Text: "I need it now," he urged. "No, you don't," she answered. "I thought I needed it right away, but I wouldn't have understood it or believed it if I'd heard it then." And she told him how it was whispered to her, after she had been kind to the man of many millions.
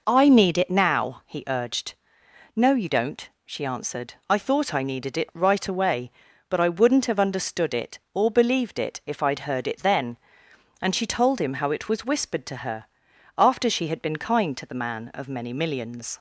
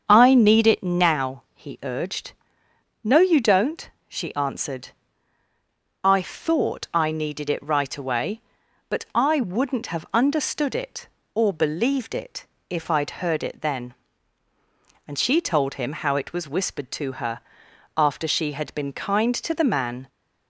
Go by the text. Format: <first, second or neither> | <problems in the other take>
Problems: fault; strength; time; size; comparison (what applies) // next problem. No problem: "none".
first | starts louder than the rest; strong; until 1.0 s; 7 dB // pauses between "it" and "if"; slight; at 12.4 s; 0.22 s long // stops before "of many millions"; at 20.0 s